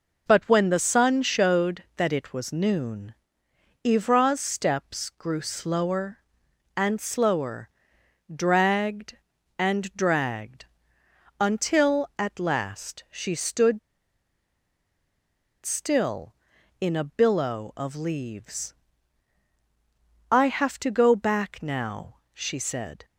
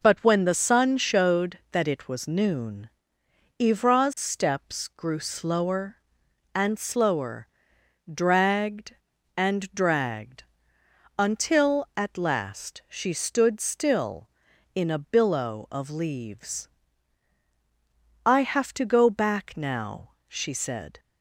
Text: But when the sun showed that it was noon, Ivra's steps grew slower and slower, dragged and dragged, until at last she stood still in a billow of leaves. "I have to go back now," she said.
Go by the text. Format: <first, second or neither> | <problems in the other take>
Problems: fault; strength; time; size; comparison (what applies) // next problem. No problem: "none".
second | pauses between "stood" and "still"; strong; at 13.7 s; 1.8 s long